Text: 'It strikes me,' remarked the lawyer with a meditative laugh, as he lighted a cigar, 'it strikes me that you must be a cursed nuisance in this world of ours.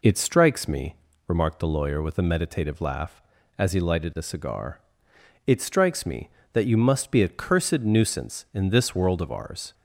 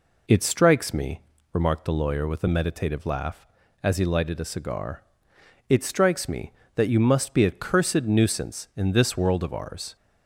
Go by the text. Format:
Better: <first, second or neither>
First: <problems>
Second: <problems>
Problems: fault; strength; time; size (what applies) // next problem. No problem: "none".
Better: neither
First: none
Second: none